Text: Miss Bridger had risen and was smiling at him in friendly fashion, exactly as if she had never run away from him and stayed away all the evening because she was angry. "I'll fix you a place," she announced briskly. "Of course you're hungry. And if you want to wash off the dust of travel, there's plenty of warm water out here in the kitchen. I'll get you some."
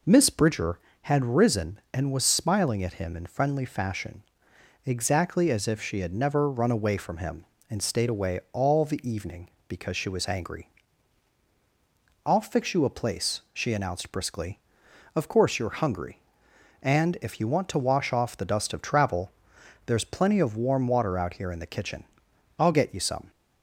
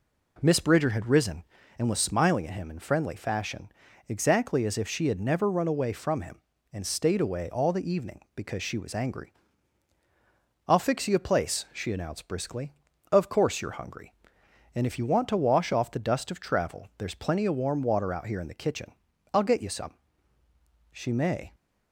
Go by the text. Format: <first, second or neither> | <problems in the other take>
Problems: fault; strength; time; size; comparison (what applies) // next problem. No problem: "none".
first | goes on to say "She may"; noticeable; from 20.9 s on; 0.64 s long